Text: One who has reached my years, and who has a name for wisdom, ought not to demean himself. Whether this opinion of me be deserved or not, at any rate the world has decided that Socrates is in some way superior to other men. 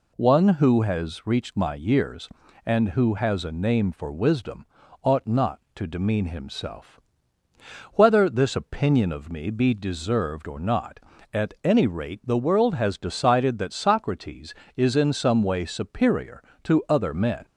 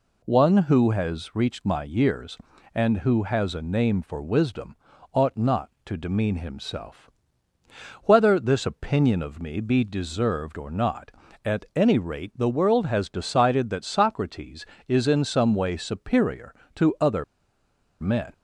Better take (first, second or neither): first